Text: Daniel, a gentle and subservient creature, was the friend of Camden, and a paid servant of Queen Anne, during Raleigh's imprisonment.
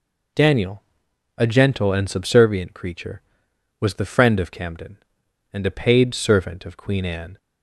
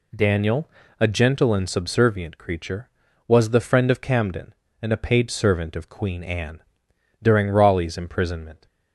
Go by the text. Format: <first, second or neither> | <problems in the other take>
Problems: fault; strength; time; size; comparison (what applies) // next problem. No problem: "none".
second | stops before "during Raleigh's imprisonment"; at 7.3 s